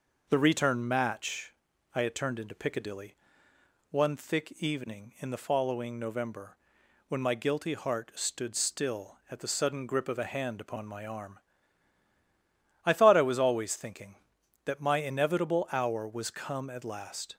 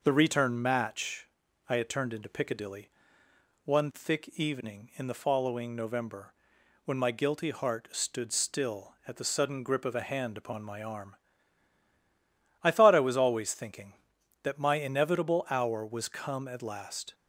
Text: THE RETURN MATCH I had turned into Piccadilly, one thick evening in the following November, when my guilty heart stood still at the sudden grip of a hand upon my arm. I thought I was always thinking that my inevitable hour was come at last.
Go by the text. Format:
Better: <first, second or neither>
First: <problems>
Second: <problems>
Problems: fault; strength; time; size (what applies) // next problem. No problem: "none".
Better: neither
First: pauses between "MATCH" and "I"; at 1.5 s; 0.42 s long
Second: pauses between "MATCH" and "I"; at 1.2 s; 0.42 s long